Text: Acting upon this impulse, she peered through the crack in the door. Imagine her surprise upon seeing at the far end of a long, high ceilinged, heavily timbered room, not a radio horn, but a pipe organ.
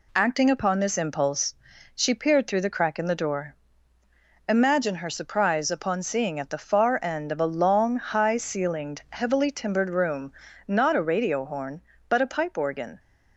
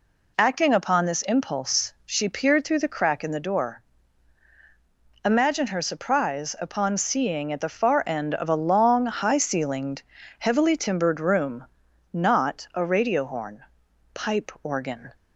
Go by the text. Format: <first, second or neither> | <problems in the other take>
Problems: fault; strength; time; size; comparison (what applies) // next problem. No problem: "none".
first | skips "but a"; at 13.8 s